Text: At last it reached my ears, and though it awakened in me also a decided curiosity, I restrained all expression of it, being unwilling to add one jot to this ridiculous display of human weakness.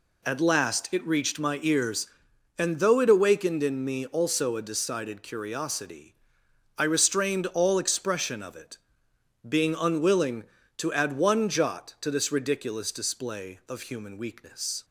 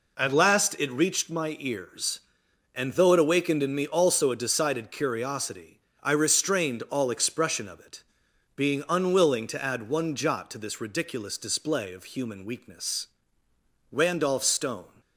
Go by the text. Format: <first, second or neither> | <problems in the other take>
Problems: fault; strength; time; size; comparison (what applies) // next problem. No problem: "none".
first | goes on to say "Randolph Stone"; noticeable; from 13.9 s on; 1.0 s long